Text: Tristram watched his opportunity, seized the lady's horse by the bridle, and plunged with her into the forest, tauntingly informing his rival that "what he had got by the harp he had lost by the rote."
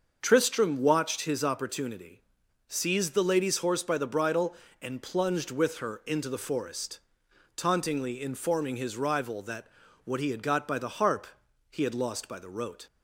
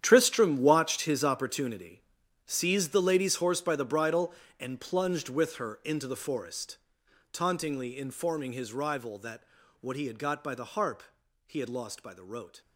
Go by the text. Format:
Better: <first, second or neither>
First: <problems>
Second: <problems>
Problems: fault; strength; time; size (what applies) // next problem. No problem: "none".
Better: first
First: starts louder than the rest; until 1.2 s; 6.5 dB // pauses between "that" and "what"; at 9.6 s; 0.38 s long // pauses between "harp" and "he"; at 11.2 s; 0.44 s long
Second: gets quieter; strong; throughout; 14 dB // starts louder than the rest; strong; until 1.0 s; 9.5 dB // pauses between "that" and "what"; at 9.4 s; 0.38 s long // pauses between "harp" and "he"; at 11.0 s; 0.44 s long